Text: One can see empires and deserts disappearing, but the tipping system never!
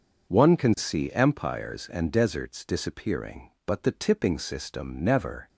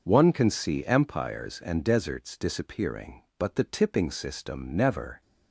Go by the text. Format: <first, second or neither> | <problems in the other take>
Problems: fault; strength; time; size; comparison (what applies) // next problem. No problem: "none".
neither | none